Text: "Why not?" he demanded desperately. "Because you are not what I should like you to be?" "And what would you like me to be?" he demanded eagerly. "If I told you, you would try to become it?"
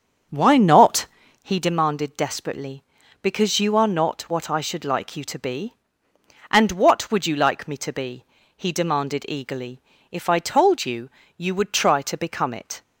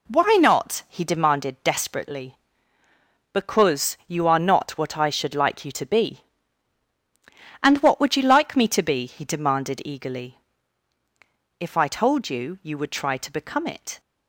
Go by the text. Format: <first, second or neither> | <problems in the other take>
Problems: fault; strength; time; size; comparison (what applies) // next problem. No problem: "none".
second | starts louder than the rest; strong; until 1.6 s; 7 dB